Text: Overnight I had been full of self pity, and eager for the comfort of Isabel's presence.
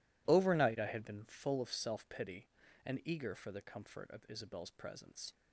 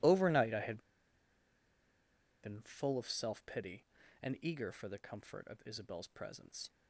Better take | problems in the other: first | pauses between "had" and "been"; strong; at 0.7 s; 1.6 s long

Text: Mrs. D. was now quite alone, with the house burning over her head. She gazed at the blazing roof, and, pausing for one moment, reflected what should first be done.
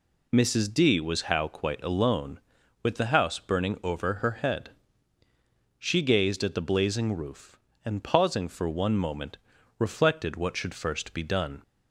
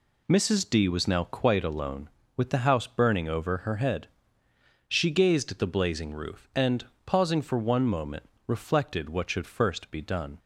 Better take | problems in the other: second | says "how" for "now"; at 1.2 s

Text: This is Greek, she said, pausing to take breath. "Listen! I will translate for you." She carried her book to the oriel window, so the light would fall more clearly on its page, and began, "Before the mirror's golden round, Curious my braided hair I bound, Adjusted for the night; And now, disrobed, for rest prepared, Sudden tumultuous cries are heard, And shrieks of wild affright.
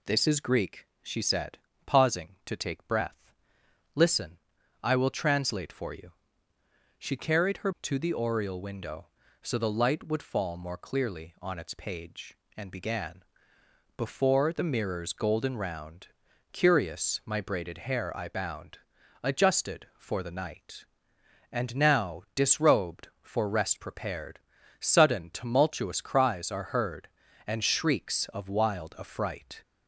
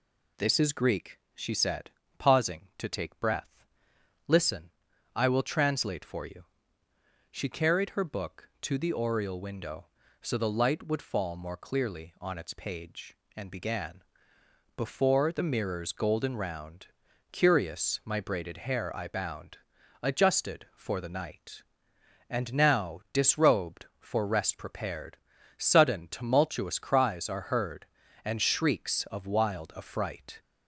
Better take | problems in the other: second | skips "book"; at 7.7 s

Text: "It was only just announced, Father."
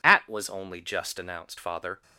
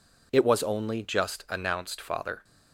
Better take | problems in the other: second | says "At" for "It"; at 0.0 s

